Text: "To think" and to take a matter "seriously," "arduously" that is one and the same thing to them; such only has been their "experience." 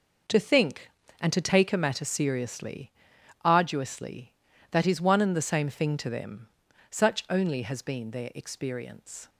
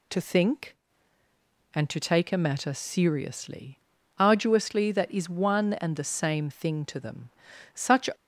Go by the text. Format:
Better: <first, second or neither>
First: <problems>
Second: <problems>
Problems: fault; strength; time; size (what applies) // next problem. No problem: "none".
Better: first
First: none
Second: stops before "only has been their experience"; at 8.1 s